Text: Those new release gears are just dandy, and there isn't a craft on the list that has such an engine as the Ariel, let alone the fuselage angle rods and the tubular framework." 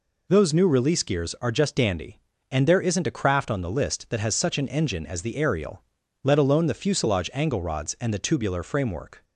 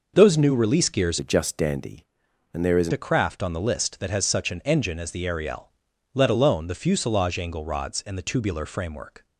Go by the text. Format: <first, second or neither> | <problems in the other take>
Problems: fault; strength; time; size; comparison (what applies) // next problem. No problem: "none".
first | changes voice from "are" to "isn't"; from 1.1 to 2.9 s; 1.8 s long